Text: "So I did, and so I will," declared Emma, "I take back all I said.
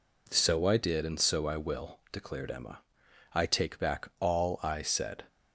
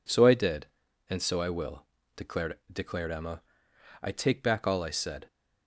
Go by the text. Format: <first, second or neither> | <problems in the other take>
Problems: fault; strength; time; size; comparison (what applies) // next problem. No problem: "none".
first | says "declared" twice; at 2.7 s